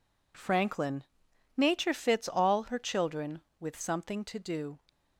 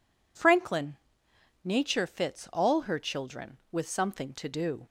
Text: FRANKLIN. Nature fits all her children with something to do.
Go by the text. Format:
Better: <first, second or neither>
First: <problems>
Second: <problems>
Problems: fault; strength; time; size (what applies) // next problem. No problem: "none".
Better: neither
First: none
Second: none